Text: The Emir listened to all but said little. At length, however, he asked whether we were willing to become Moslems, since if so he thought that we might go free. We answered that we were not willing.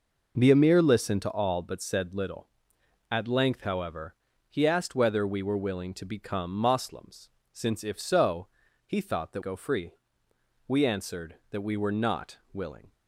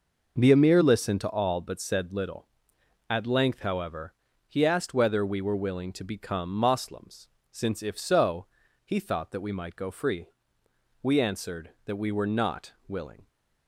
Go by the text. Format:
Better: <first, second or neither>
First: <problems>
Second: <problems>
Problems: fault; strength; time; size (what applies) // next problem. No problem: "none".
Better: second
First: pauses between "so" and "he"; at 8.4 s; 0.38 s long // skips "we might"; at 9.4 s // pauses between "not" and "willing"; slight; at 12.3 s; 0.16 s long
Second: pauses between "so" and "he"; at 8.4 s; 0.38 s long // pauses between "not" and "willing"; slight; at 12.7 s; 0.16 s long